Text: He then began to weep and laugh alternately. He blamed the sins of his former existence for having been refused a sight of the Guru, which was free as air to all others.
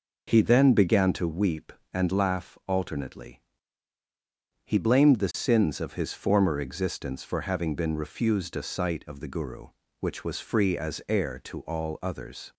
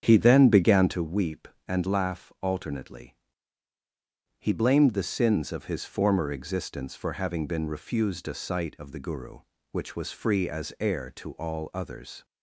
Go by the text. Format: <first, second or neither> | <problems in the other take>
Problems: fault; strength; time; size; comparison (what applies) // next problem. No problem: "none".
first | starts louder than the rest; strong; until 1.0 s; 8 dB